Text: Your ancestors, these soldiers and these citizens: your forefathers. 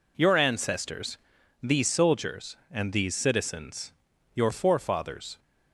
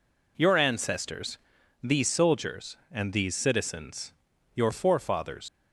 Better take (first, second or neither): first